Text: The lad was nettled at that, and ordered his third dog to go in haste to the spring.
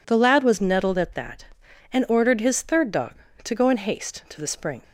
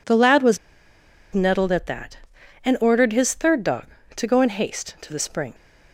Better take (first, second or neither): first